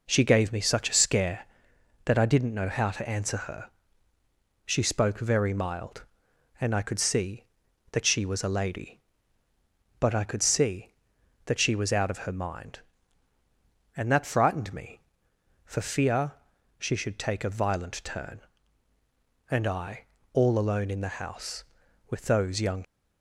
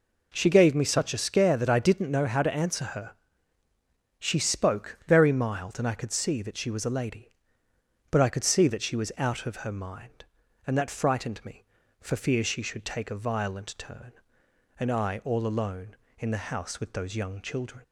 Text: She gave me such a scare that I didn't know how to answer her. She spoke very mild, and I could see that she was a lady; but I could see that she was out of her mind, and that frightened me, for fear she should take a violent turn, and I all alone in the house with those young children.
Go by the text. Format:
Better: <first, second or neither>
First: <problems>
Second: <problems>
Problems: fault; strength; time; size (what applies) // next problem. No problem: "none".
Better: second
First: pauses between "fear" and "she"; noticeable; at 16.3 s; 0.46 s long // pauses between "I" and "all"; slight; at 20.0 s; 0.28 s long // stops before "children"; at 22.8 s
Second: none